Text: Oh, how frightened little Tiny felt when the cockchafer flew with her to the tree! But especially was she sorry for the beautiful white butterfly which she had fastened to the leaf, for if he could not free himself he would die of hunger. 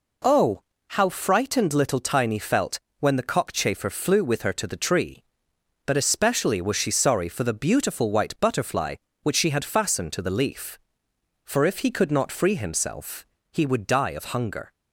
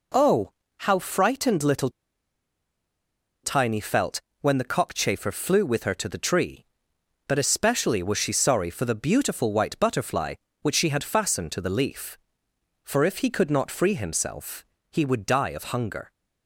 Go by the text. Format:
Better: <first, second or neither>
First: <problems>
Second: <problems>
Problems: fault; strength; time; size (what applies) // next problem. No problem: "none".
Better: first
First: pauses between "felt" and "when"; slight; at 2.7 s; 0.22 s long // pauses between "himself" and "he"; slight; at 13.2 s; 0.28 s long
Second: pauses between "little" and "Tiny"; strong; at 1.8 s; 1.5 s long // pauses between "felt" and "when"; slight; at 4.2 s; 0.22 s long // pauses between "himself" and "he"; slight; at 14.6 s; 0.28 s long